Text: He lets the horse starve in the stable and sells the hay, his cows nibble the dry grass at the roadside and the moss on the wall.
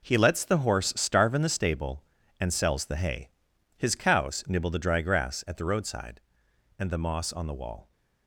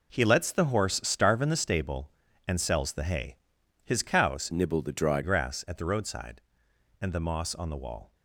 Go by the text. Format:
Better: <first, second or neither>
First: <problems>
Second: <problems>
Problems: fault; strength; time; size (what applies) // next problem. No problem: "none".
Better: first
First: none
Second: changes voice from "nibble" to "dry"; from 4.5 to 5.2 s; 0.7 s long